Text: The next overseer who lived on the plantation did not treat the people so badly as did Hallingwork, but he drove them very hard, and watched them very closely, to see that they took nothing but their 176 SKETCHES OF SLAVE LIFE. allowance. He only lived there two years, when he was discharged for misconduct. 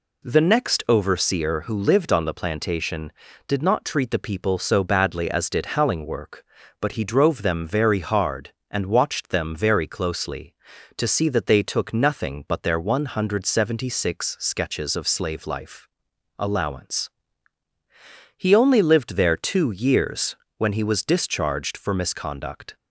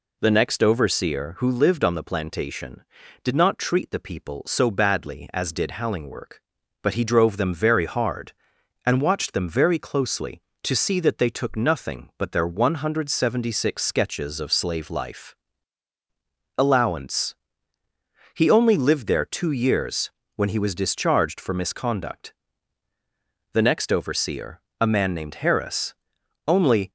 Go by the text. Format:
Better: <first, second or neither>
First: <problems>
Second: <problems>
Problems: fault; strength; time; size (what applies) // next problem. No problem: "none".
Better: first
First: none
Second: goes on to say "The next overseer a man named Harris only"; strong; from 23.5 s on; 3.3 s long